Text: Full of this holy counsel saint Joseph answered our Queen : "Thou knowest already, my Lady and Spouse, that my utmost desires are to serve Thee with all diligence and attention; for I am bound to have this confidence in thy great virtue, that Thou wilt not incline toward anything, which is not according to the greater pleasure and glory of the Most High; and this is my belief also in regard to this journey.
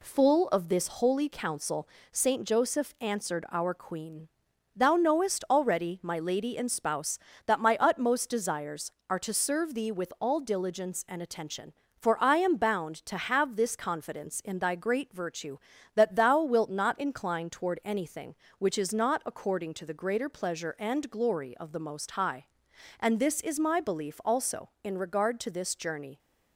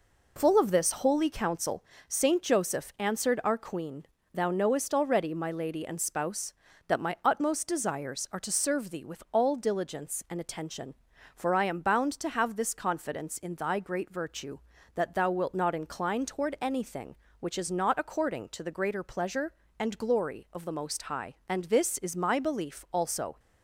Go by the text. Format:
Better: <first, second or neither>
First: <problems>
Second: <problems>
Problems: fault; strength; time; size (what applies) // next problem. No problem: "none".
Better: first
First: pauses between "counsel" and "saint"; slight; at 1.8 s; 0.22 s long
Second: pauses between "counsel" and "saint"; slight; at 1.8 s; 0.24 s long // stops before "in regard to this journey"; at 23.3 s